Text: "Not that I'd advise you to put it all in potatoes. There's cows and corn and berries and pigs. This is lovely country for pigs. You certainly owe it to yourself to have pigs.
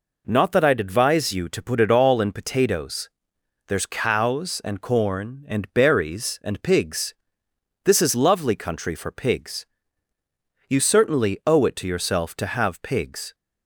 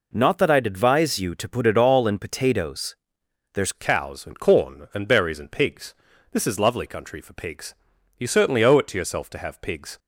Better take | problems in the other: first | changes voice at "cows"; from 3.7 s on; 6.2 s long

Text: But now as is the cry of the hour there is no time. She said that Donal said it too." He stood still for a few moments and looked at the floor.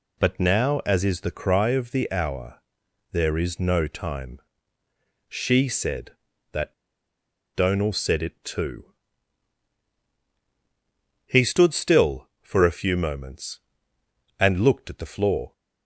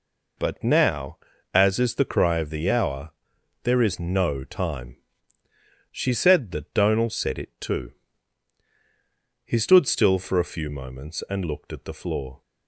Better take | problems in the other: second | pauses between "hour" and "there"; noticeable; at 2.5 s; 0.56 s long; noticeable in the second // pauses between "that" and "Donal"; noticeable; at 6.7 s; 0.81 s long

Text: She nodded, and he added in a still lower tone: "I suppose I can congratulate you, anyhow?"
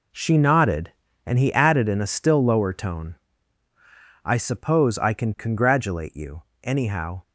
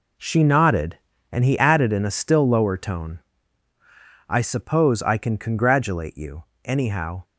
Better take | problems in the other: neither | none

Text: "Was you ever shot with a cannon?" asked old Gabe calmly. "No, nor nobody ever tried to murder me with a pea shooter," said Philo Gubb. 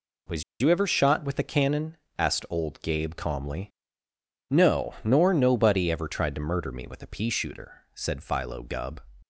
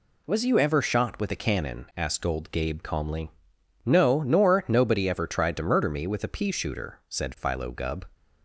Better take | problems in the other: second | pauses between "Was" and "you"; slight; at 0.4 s; 0.17 s long

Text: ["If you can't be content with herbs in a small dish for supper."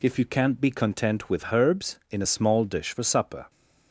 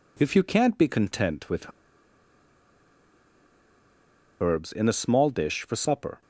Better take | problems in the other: first | pauses between "with" and "herbs"; strong; at 1.7 s; 2.6 s long

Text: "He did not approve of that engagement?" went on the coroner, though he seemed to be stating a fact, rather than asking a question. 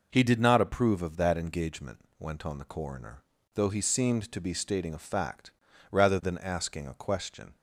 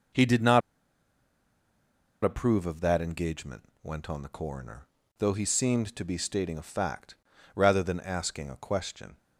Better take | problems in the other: first | pauses between "not" and "approve"; strong; at 0.6 s; 1.6 s long

